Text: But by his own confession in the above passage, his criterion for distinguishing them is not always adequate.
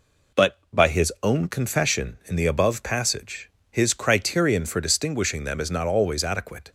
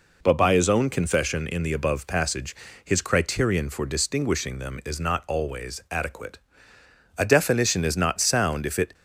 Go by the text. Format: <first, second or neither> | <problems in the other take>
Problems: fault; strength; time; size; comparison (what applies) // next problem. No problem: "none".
first | goes on to say "A definition is not sound if it"; strong; from 7.1 s on; 1.7 s long